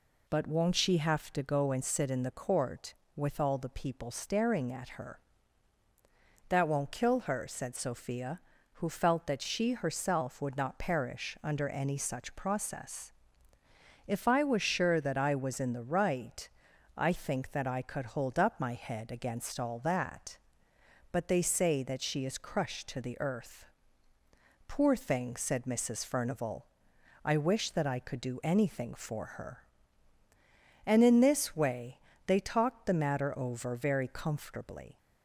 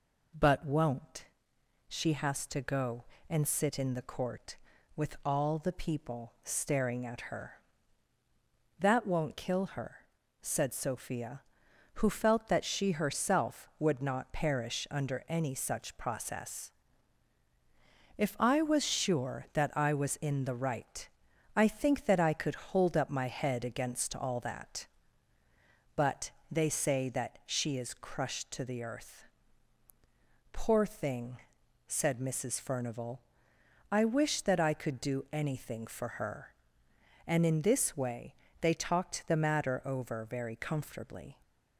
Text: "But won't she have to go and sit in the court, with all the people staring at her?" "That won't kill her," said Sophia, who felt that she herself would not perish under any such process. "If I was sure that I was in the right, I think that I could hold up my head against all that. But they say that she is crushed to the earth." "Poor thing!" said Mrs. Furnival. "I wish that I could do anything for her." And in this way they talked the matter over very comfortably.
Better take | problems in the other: first | pauses between "won't" and "she"; noticeable; at 1.2 s; 0.62 s long // says "has" for "have"; at 2.1 s // pauses between "But" and "they"; slight; at 26.3 s; 0.18 s long // pauses between "way" and "they"; slight; at 38.3 s; 0.26 s long; slight in the first

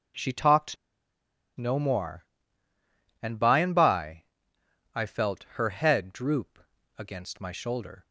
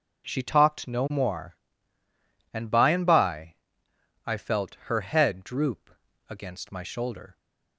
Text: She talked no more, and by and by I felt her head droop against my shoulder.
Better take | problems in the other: second | pauses between "talked" and "no"; noticeable; at 0.7 s; 0.81 s long // pauses between "by" and "I"; noticeable; at 4.2 s; 0.70 s long; noticeable in the second // pauses between "droop" and "against"; at 6.5 s; 0.38 s long; also in the second

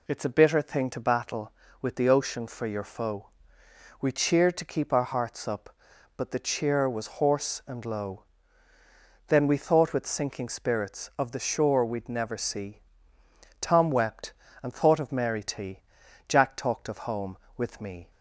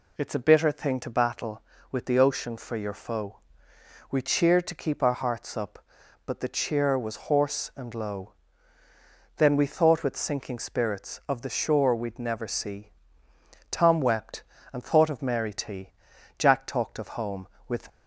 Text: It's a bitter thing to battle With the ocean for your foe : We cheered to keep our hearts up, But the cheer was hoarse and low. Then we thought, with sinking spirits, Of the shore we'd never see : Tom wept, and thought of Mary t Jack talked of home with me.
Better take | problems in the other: first | pauses between "t" and "Jack"; noticeable; at 15.8 s; 0.48 s long; noticeable in the first // stops before "me"; at 17.8 s

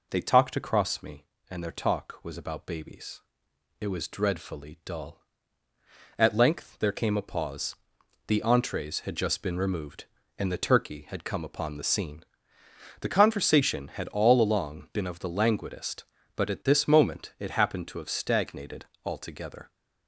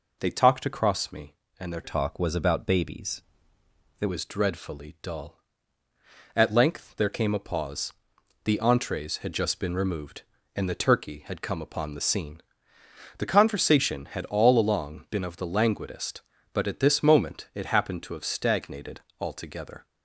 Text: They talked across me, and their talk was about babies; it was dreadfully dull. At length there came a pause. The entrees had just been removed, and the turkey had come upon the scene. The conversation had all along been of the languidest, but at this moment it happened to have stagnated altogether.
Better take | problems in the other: first | changes voice from "talk" to "it"; from 1.8 to 4.0 s; 2.2 s long // pauses between "stagnated" and "altogether"; slight; at 19.0 s; 0.18 s long; slight in the first

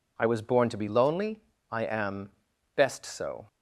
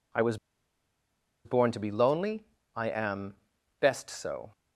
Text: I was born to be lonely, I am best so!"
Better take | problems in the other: first | pauses between "was" and "born"; at 0.3 s; 1.0 s long // pauses between "am" and "best"; noticeable; at 3.3 s; 0.46 s long; noticeable in the first

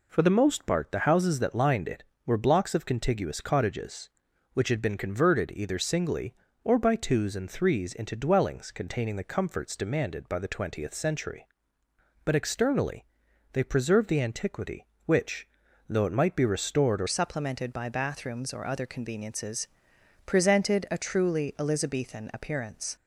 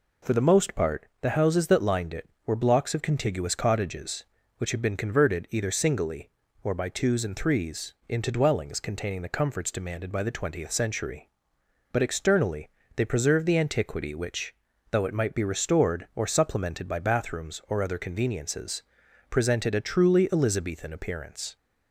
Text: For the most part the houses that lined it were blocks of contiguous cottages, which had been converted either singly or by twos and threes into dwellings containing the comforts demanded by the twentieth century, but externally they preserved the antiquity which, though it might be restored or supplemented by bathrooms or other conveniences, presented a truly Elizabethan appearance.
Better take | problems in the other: second | pauses between "externally" and "they"; noticeable; at 13.0 s; 0.48 s long; slight in the second // changes voice at "supplemented"; from 17.0 s on; 5.9 s long

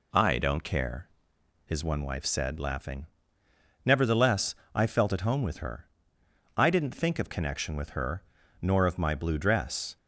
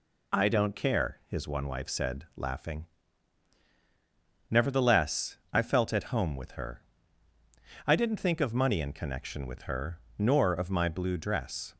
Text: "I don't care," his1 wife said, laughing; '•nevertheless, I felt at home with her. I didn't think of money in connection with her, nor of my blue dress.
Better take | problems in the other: second | skips "money in"; at 7.2 s

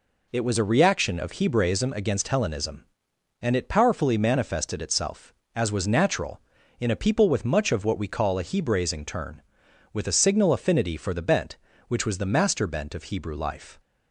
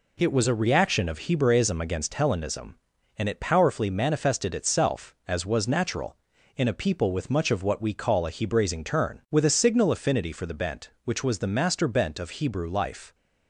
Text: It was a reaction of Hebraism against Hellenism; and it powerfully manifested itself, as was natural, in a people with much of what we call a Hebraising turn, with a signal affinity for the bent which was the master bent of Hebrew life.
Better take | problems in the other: neither | none

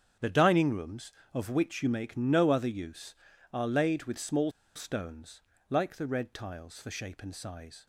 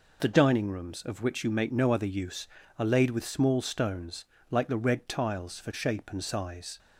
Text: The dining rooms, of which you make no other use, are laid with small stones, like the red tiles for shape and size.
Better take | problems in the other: second | starts louder than the rest; strong; until 1.4 s; 8.5 dB // pauses between "small" and "stones"; slight; at 4.4 s; 0.25 s long

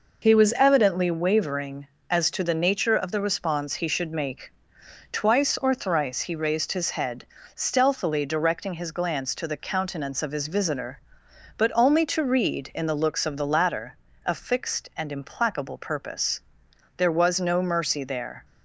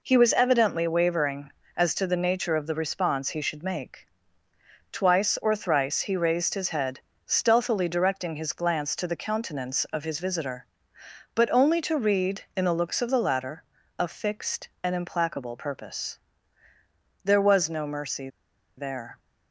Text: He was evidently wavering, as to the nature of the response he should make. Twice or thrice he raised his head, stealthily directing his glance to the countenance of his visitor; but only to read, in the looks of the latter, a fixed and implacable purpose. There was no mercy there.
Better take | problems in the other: first | pauses between "mercy" and "there"; noticeable; at 18.2 s; 0.49 s long

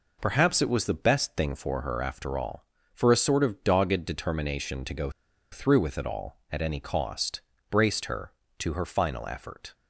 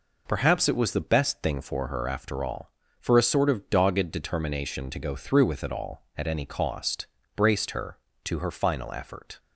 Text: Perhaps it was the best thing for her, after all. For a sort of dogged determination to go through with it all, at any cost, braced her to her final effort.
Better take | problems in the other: second | pauses between "go" and "through"; at 5.0 s; 0.42 s long

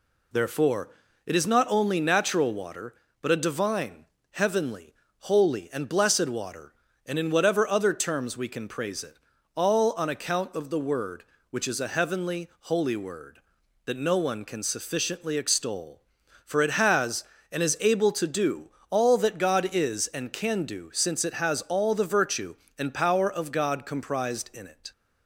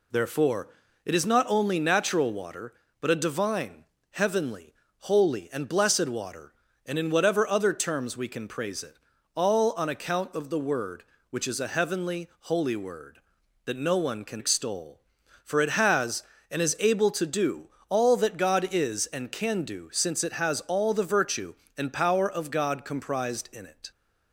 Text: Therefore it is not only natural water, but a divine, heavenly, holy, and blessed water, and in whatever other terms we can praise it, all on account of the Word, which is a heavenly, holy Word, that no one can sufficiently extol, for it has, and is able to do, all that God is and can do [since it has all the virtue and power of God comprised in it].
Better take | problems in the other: first | pauses between "Therefore" and "it"; slight; at 0.6 s; 0.36 s long; slight in the first // skips "sufficiently"; at 14.4 s

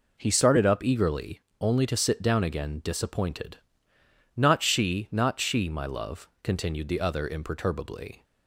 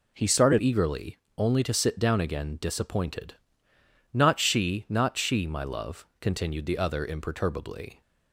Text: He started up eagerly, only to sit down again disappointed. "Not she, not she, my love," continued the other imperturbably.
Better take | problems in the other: first | skips "up"; at 0.5 s

